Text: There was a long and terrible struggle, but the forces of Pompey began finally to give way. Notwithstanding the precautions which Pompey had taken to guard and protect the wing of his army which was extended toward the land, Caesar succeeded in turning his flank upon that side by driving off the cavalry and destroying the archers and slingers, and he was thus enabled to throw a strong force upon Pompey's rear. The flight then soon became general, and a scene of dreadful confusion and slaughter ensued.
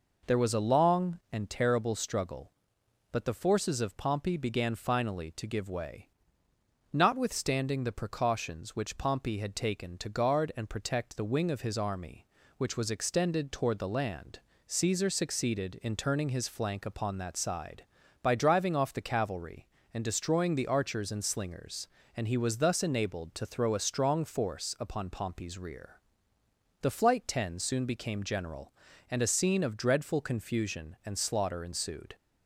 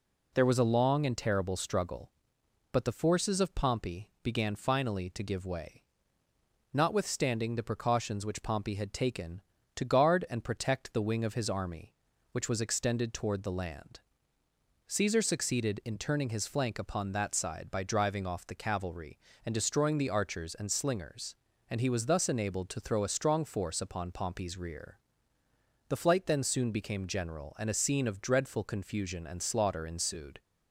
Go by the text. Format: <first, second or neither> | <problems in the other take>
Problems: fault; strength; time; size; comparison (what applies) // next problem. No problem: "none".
second | says "ten" for "then"; at 27.2 s